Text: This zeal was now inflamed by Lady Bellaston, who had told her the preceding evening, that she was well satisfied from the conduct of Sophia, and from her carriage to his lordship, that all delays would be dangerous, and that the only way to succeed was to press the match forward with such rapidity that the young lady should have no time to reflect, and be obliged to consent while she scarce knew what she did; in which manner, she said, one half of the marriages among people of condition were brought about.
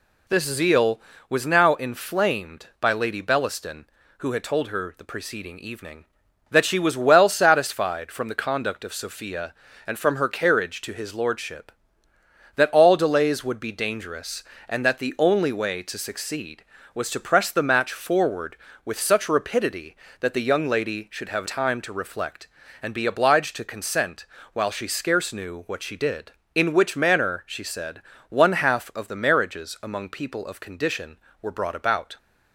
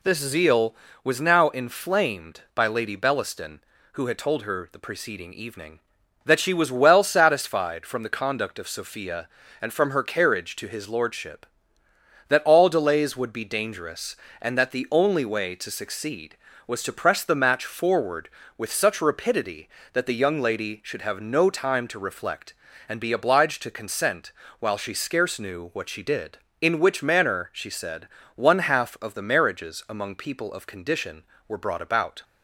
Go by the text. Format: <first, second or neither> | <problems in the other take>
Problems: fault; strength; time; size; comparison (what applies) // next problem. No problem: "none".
second | skips "no"; at 21.4 s // pauses between "consent" and "while"; slight; at 24.2 s; 0.28 s long; slight in the second